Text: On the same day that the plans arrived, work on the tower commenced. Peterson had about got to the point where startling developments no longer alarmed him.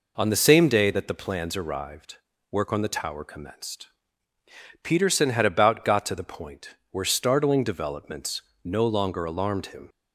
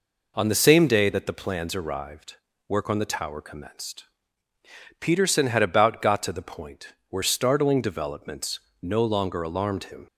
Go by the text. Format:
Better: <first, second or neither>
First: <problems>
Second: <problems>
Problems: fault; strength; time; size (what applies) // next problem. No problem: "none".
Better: neither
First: pauses between "point" and "where"; slight; at 6.7 s; 0.16 s long // pauses between "developments" and "no"; slight; at 8.4 s; 0.22 s long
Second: pauses between "point" and "where"; slight; at 6.9 s; 0.16 s long // pauses between "developments" and "no"; slight; at 8.5 s; 0.22 s long